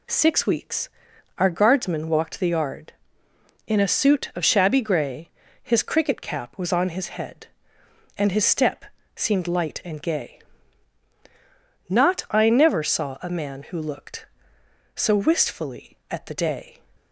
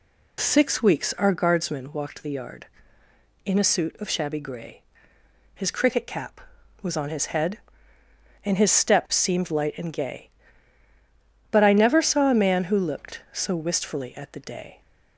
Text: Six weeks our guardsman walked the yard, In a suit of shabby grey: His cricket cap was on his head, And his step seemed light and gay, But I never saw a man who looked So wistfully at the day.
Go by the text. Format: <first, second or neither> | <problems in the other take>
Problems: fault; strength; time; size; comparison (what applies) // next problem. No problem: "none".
second | pauses between "weeks" and "our"; noticeable; at 0.8 s; 0.50 s long // pauses between "step" and "seemed"; slight; at 8.8 s; 0.30 s long // says "Not" for "But"; at 11.8 s